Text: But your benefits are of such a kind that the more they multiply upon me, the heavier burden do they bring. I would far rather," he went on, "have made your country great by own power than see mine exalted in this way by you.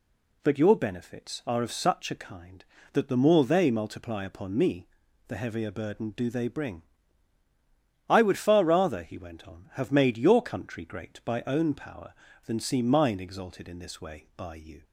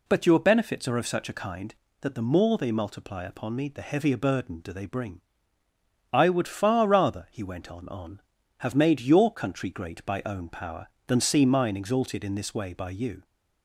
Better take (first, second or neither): first